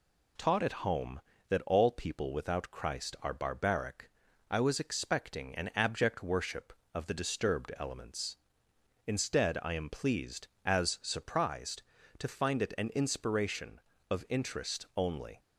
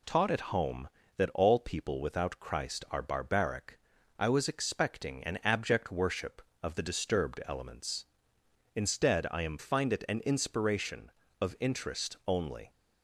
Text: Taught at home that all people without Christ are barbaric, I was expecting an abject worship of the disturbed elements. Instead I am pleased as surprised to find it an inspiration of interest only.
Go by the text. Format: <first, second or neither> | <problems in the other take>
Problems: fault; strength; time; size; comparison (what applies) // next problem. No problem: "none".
first | skips "pleased as surprised to"; at 9.5 s